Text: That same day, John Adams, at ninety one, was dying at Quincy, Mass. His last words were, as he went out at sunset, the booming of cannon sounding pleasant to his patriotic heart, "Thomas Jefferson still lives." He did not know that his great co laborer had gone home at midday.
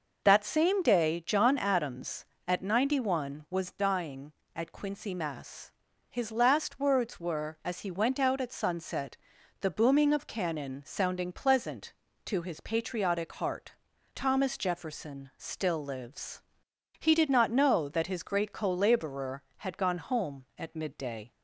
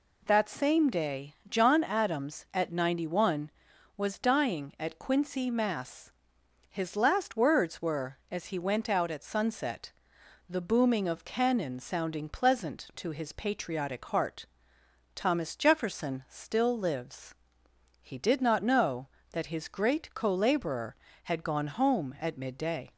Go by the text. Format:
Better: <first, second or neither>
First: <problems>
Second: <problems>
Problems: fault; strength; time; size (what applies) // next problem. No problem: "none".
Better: neither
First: none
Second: none